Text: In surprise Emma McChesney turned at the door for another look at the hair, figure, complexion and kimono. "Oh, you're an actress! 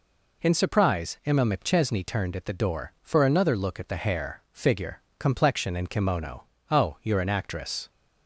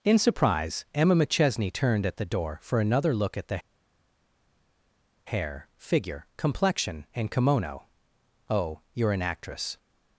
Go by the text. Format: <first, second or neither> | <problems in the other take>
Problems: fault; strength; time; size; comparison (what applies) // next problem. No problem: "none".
first | pauses between "the" and "hair"; strong; at 3.5 s; 1.6 s long